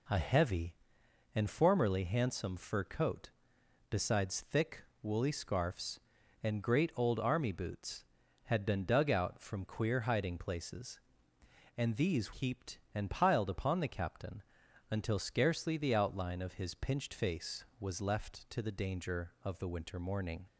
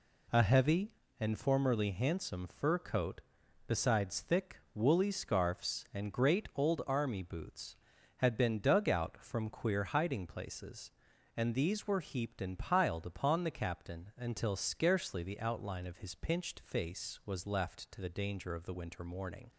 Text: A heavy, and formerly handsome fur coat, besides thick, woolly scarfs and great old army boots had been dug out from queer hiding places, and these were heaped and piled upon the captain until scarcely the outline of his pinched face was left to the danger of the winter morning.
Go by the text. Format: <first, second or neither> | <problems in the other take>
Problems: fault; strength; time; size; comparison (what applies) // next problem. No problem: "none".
second | skips "were"; at 12.3 s // pauses between "captain" and "until"; noticeable; at 14.4 s; 0.48 s long